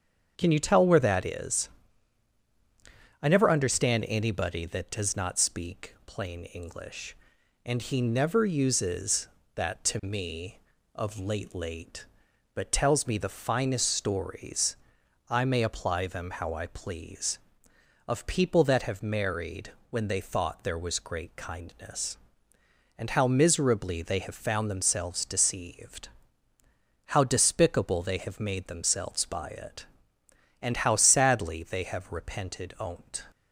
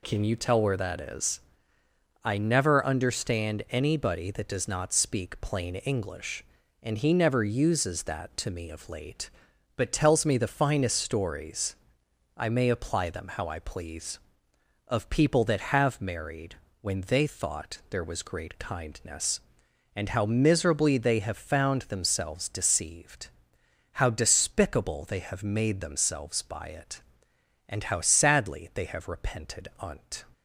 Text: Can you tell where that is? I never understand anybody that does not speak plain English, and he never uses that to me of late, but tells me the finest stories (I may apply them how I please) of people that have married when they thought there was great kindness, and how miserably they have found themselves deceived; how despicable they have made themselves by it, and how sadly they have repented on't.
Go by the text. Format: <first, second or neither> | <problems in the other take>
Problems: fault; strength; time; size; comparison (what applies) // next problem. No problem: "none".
second | starts louder than the rest; strong; until 1.3 s; 7.5 dB // says "late" twice; at 11.5 s // pauses between "married" and "when"; slight; at 19.7 s; 0.20 s long; slight in the second